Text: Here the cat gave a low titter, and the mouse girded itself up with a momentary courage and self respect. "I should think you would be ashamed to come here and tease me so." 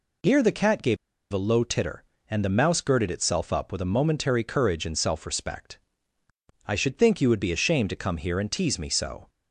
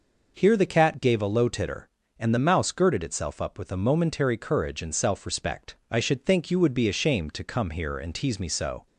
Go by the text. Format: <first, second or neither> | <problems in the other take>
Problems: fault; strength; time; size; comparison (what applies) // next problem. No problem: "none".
second | pauses between "gave" and "a"; at 0.9 s; 0.36 s long